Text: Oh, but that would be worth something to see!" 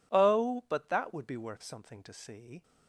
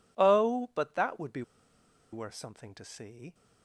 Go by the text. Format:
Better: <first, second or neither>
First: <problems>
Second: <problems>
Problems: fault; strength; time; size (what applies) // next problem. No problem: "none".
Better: first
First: none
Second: pauses between "be" and "worth"; noticeable; at 1.4 s; 0.70 s long